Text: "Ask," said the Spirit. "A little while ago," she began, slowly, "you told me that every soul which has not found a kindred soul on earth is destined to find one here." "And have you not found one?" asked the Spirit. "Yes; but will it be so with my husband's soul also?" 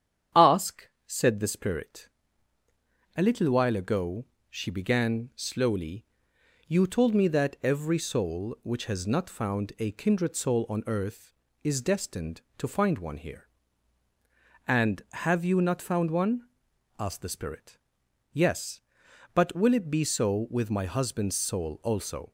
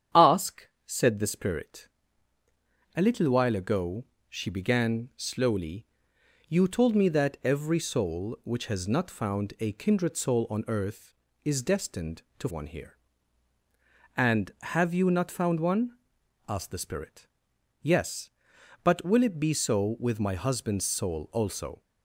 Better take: first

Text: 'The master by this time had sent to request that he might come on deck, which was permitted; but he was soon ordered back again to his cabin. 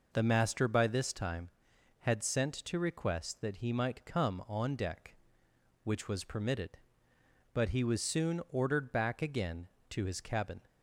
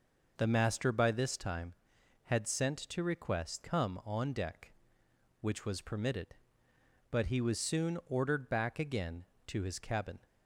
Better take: first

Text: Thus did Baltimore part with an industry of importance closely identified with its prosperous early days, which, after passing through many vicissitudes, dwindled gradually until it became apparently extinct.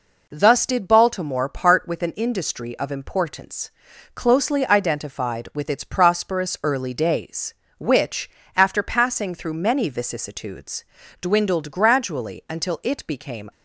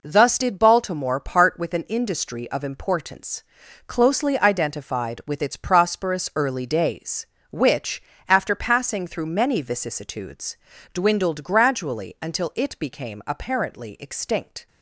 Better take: second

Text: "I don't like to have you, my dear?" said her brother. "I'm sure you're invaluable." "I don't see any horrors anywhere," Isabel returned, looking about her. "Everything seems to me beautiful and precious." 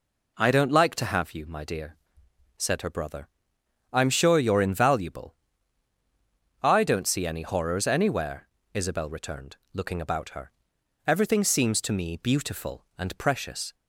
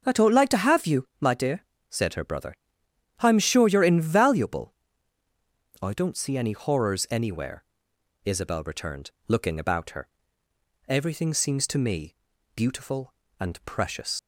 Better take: first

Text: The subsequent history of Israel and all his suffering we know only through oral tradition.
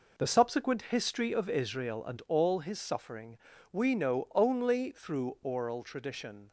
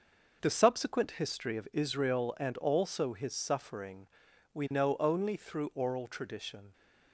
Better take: first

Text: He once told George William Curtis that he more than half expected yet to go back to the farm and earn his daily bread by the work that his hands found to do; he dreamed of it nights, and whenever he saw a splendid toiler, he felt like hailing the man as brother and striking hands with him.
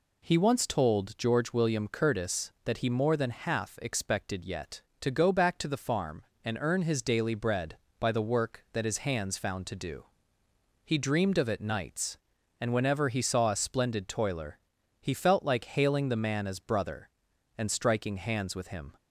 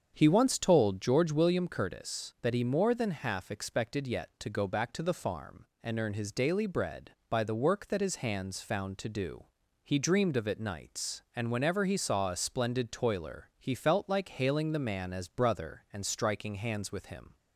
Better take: first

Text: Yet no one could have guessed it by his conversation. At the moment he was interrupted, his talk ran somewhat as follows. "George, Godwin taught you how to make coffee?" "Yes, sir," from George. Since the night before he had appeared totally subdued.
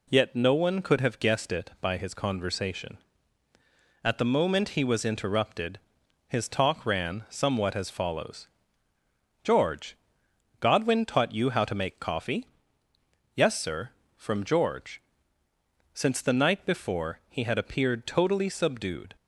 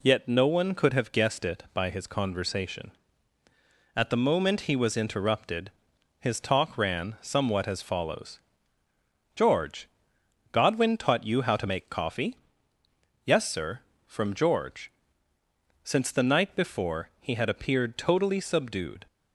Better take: neither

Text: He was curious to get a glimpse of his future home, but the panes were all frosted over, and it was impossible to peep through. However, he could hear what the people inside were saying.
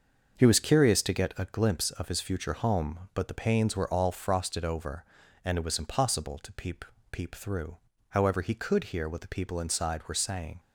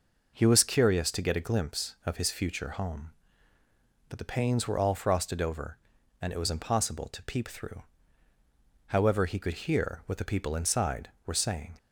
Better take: second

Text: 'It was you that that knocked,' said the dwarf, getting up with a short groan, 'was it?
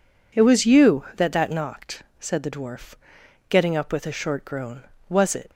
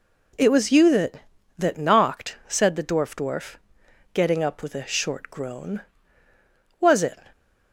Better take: first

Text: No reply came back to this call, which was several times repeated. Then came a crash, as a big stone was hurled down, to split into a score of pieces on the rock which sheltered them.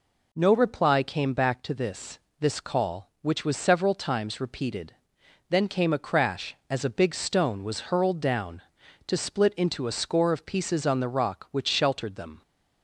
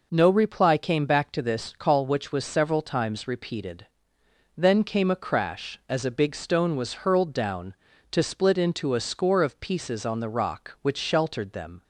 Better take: second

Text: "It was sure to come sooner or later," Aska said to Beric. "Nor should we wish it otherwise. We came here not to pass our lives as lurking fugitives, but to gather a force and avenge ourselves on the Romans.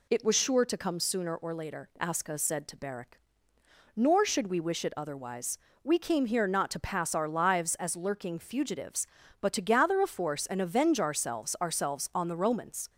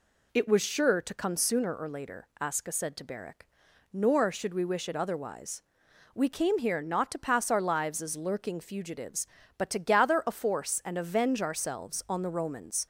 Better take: second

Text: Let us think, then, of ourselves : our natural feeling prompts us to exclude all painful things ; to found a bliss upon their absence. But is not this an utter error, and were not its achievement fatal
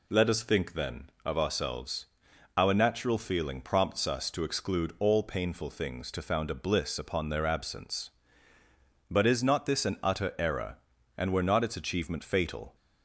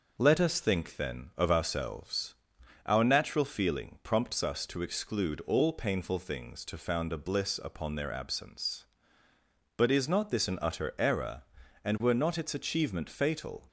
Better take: neither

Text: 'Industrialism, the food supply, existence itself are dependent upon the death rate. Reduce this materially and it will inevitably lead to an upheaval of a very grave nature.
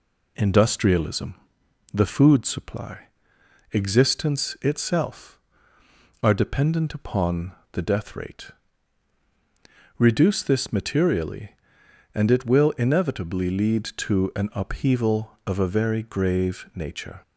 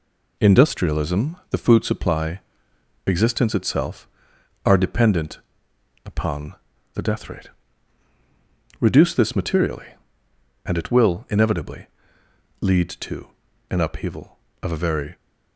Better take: first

